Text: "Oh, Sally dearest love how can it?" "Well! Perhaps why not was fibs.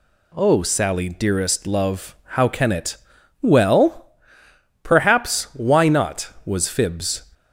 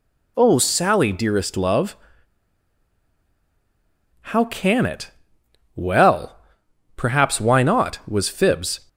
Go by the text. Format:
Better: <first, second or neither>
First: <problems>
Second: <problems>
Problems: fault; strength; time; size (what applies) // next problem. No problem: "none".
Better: first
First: none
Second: pauses between "love" and "how"; strong; at 1.9 s; 2.3 s long